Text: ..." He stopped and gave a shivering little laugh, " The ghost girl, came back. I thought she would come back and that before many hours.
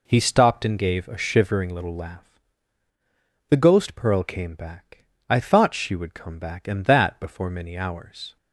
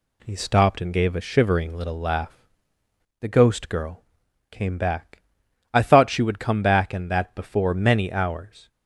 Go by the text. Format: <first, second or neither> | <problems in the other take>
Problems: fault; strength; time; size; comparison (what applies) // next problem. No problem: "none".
second | says "pearl" for "girl"; at 3.9 s